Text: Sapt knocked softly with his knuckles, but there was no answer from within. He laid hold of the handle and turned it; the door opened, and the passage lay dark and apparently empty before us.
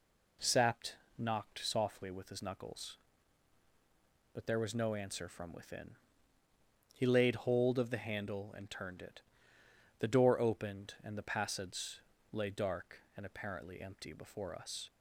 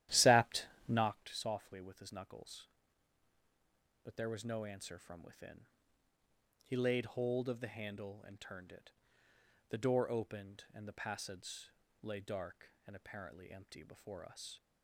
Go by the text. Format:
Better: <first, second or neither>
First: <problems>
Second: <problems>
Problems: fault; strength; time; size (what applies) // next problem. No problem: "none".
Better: first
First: pauses between "Sapt" and "knocked"; slight; at 0.9 s; 0.22 s long // pauses between "passage" and "lay"; slight; at 11.9 s; 0.32 s long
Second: starts louder than the rest; strong; until 1.3 s; 13 dB // pauses between "Sapt" and "knocked"; slight; at 0.6 s; 0.22 s long // pauses between "passage" and "lay"; slight; at 11.6 s; 0.32 s long